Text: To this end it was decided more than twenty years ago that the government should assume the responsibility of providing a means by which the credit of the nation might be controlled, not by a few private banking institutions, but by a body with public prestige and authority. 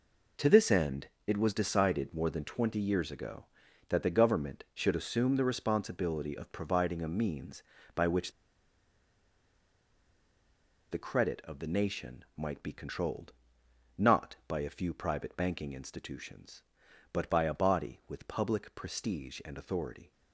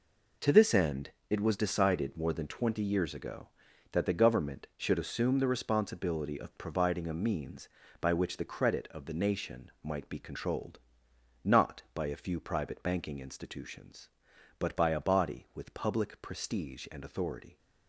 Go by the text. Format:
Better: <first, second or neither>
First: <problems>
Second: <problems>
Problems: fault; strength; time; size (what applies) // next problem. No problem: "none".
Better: second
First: pauses between "end" and "it"; slight; at 1.0 s; 0.20 s long // pauses between "which" and "the"; strong; at 8.3 s; 2.5 s long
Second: pauses between "end" and "it"; slight; at 1.1 s; 0.20 s long